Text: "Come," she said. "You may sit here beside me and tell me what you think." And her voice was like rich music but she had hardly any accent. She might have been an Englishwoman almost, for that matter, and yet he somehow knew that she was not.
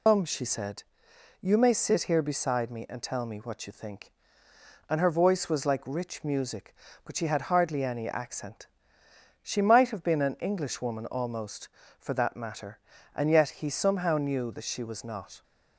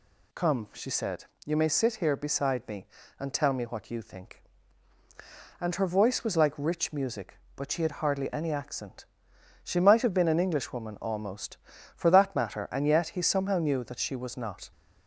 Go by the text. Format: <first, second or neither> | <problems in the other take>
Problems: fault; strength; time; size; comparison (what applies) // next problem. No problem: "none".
second | loses the start of "Come"; at 0.0 s; 135 ms